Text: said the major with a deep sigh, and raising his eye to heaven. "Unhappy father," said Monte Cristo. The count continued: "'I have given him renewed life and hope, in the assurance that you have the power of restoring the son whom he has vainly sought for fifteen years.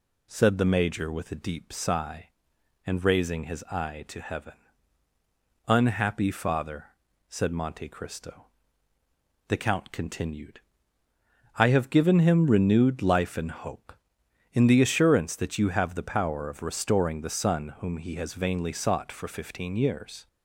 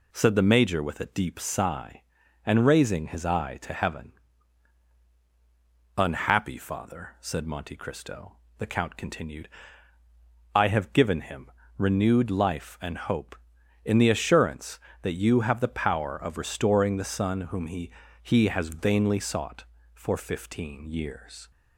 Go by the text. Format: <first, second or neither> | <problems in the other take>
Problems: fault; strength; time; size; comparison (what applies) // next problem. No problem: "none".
first | pauses between "him" and "renewed"; slight; at 11.5 s; 0.26 s long // says "he" twice; at 18.2 s